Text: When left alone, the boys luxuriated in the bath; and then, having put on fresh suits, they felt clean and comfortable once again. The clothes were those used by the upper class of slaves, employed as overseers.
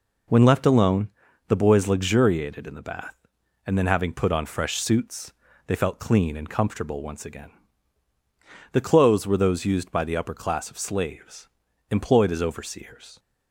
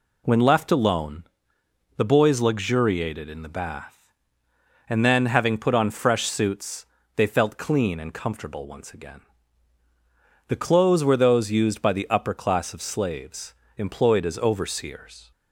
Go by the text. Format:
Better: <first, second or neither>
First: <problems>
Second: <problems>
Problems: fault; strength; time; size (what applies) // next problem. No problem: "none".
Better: neither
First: none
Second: none